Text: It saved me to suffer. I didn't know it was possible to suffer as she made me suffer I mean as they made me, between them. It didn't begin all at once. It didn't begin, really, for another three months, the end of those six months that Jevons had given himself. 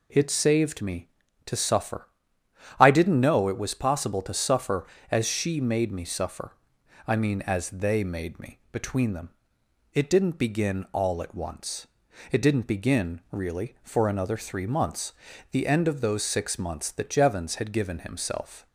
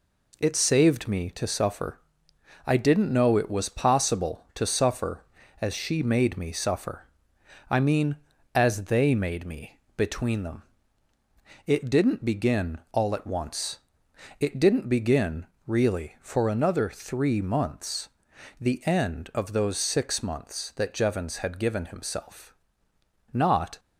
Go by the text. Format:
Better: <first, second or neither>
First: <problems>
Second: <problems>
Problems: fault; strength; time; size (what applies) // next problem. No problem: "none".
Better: first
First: pauses between "suffer" and "I"; noticeable; at 6.5 s; 0.56 s long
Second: pauses between "suffer" and "I"; noticeable; at 7.0 s; 0.66 s long // goes on to say "Not"; slight; from 23.3 s on; 0.46 s long